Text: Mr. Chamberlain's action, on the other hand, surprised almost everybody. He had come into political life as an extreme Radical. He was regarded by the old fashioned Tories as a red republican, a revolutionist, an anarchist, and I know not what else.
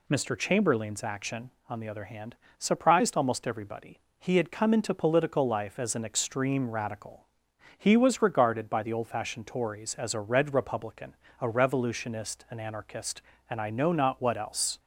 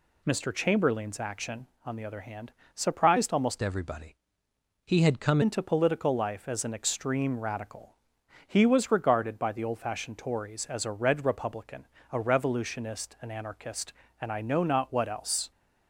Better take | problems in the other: first | changes voice from "everybody" to "come"; from 3.5 to 5.3 s; 1.8 s long

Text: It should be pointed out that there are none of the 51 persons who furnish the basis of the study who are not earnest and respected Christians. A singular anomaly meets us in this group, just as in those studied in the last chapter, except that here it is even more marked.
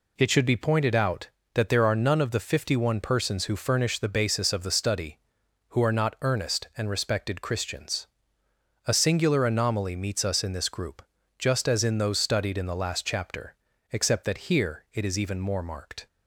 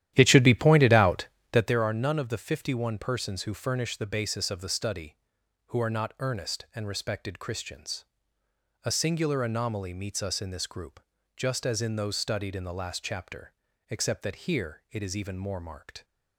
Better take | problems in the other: first | starts louder than the rest; strong; until 1.8 s; 12 dB

